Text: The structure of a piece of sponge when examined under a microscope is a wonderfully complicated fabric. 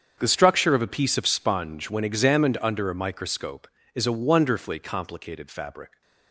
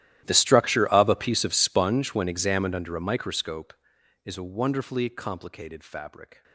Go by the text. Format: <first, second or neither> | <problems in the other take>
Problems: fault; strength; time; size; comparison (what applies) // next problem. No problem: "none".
first | gets quieter; strong; throughout; 23 dB // starts louder than the rest; strong; until 1.2 s; 13 dB; strong in the first